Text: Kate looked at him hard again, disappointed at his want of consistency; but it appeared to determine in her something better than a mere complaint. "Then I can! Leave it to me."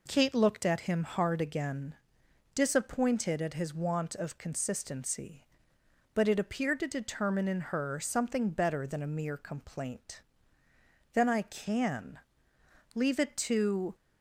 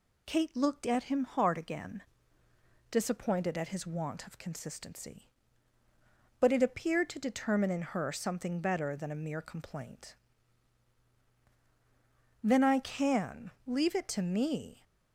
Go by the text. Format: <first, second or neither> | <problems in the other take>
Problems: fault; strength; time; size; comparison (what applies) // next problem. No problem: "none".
second | stops before "me"; at 13.9 s